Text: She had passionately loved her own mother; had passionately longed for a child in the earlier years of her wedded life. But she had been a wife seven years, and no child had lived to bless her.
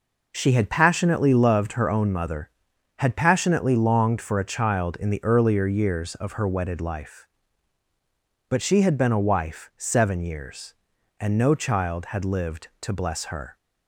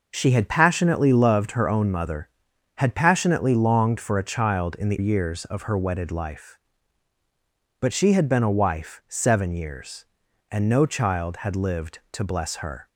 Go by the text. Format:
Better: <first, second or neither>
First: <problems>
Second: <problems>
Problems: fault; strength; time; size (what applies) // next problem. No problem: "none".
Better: first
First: none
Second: skips "earlier"; at 4.9 s